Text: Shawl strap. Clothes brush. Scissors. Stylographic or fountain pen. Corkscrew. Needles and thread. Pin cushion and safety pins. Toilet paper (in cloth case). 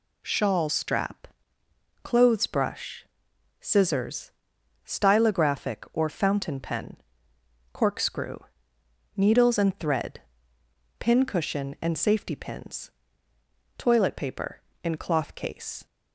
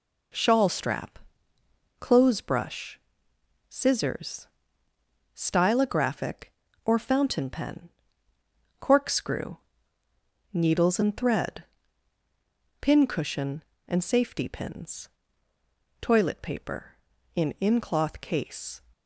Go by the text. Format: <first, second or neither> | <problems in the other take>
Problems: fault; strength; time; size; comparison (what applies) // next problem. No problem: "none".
first | says "in" twice; at 17.6 s